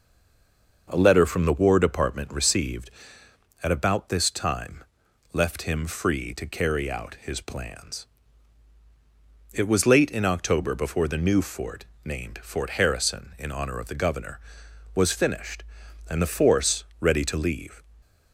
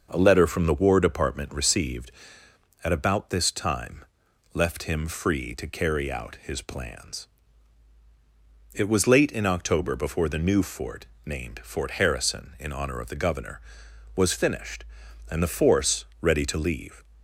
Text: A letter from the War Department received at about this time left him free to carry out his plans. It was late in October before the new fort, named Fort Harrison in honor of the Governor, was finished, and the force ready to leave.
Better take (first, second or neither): second